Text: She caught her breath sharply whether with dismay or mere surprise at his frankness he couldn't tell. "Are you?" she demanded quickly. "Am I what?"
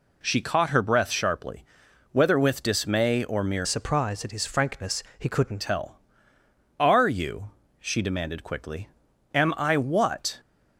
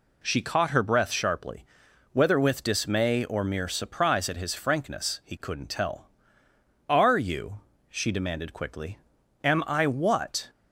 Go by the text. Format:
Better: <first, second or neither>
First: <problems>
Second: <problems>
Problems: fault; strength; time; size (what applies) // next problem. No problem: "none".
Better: second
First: pauses between "sharply" and "whether"; noticeable; at 1.6 s; 0.48 s long // changes voice from "surprise" to "couldn't"; from 3.6 to 5.6 s; 2.0 s long // pauses between "frankness" and "he"; slight; at 5.0 s; 0.16 s long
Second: pauses between "sharply" and "whether"; noticeable; at 1.6 s; 0.48 s long